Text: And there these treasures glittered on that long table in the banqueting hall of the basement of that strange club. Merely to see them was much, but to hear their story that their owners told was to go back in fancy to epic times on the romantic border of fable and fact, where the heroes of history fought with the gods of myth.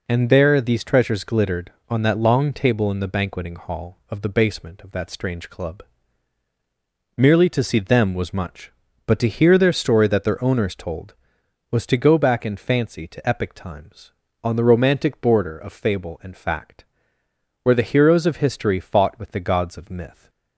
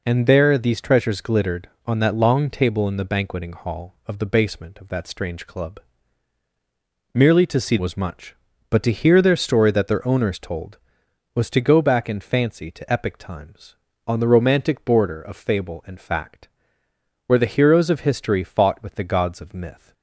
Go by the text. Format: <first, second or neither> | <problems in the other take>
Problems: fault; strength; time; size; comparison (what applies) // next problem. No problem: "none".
first | skips "them"; at 7.7 s